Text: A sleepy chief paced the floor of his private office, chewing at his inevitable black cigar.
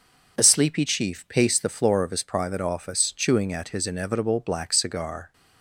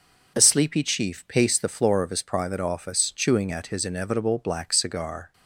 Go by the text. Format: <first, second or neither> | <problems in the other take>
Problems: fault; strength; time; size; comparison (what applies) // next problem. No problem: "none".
neither | none